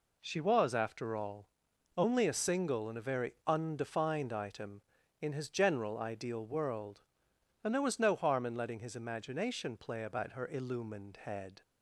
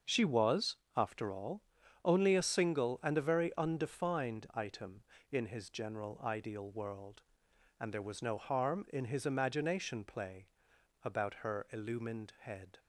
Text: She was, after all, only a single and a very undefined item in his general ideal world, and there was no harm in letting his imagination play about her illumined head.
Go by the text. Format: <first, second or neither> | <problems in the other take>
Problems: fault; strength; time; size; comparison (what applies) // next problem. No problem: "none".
first | starts louder than the rest; until 1.2 s; 6.5 dB // skips "letting"; at 9.0 s // pauses between "play" and "about"; noticeable; at 10.4 s; 0.56 s long